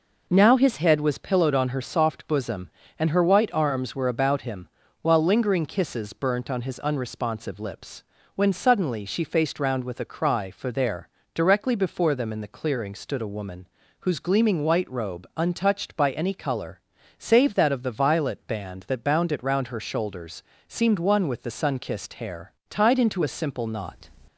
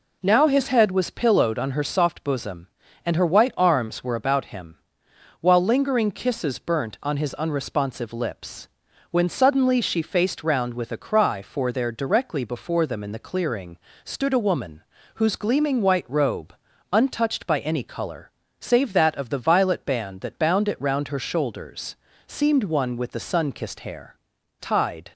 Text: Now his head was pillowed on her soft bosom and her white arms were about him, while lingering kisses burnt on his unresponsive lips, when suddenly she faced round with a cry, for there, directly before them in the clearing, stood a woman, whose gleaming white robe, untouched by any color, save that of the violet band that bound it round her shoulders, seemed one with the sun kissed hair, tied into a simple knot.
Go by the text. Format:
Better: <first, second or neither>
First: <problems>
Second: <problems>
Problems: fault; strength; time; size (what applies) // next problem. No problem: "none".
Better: first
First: none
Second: stops before "into a simple knot"; at 25.1 s